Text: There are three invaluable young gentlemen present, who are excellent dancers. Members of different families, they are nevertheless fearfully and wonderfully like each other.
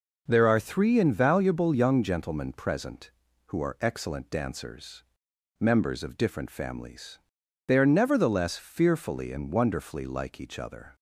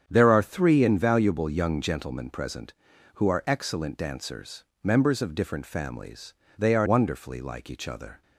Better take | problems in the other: first | starts louder than the rest; strong; until 1.0 s; 8.5 dB // skips "nevertheless fearfully and"; at 6.8 s

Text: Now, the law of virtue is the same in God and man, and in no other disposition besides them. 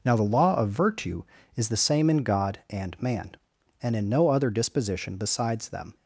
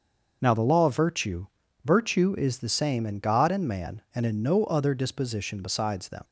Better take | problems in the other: first | starts louder than the rest; until 1.4 s; 6.5 dB // says "virtue" twice; at 1.8 s

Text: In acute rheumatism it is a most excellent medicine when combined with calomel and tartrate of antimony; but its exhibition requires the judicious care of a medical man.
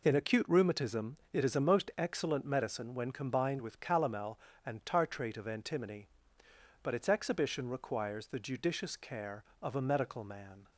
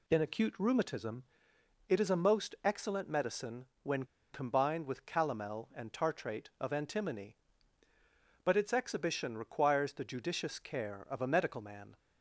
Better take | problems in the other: first | pauses between "rheumatism" and "it"; noticeable; at 1.2 s; 0.64 s long; slight in the first // pauses between "medicine" and "when"; slight; at 3.6 s; 0.18 s long // pauses between "when" and "combined"; slight; at 4.0 s; 0.27 s long

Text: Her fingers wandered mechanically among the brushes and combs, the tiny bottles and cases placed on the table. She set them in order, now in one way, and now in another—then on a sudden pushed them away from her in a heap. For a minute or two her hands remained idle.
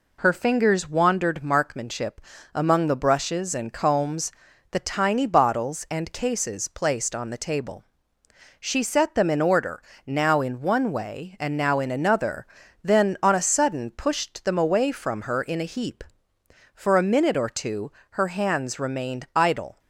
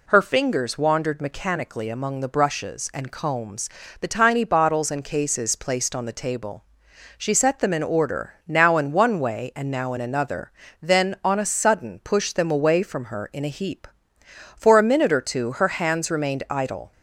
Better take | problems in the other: second | says "markmanship" for "mechanically"; at 1.4 s // pauses between "two" and "her"; slight; at 17.9 s; 0.18 s long

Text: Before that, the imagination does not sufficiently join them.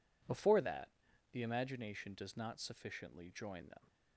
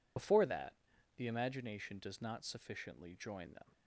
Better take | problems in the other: first | loses the start of "Before"; at 0.1 s; 90 ms

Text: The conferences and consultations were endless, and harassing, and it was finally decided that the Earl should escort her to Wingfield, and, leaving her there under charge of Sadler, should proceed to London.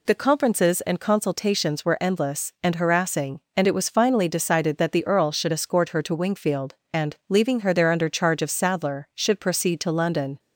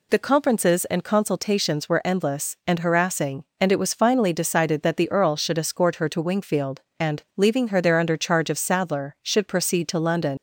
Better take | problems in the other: first | leaves "London" unfinished; at 10.3 s; 90 ms

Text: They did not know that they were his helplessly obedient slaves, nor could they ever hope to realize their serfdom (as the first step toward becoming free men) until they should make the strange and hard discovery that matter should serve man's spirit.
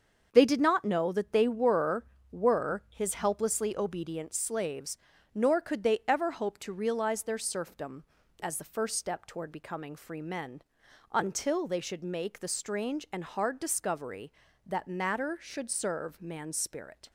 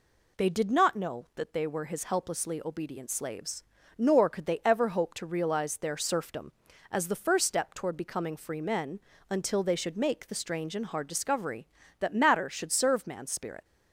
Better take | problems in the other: second | starts louder than the rest; until 1.3 s; 6.5 dB // says "were" twice; at 2.3 s

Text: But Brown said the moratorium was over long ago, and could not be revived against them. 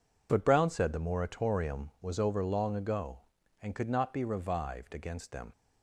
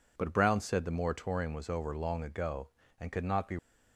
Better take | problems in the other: first | stops before "revived against them"; at 3.5 s

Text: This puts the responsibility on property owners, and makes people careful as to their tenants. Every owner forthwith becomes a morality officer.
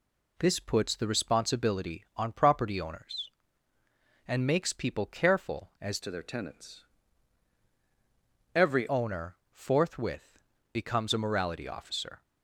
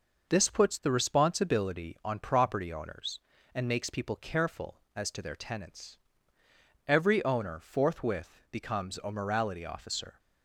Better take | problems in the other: second | changes voice from "to" to "Every"; from 6.0 to 8.8 s; 2.8 s long // pauses between "owner" and "forthwith"; slight; at 9.3 s; 0.16 s long // pauses between "forthwith" and "becomes"; slight; at 10.3 s; 0.36 s long

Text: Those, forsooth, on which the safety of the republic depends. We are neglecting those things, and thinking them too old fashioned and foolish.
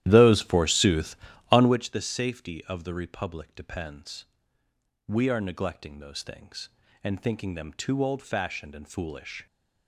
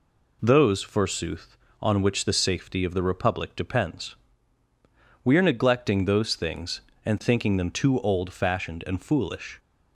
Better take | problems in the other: second | starts louder than the rest; strong; until 1.8 s; 13 dB

